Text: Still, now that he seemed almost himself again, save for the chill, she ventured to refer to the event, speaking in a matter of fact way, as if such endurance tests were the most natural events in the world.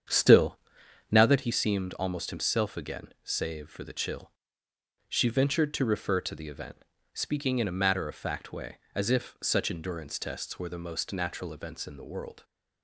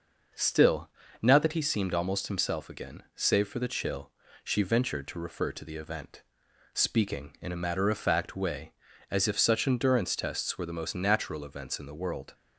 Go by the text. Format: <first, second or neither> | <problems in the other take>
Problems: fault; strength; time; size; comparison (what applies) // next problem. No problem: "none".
second | starts louder than the rest; strong; until 1.4 s; 8 dB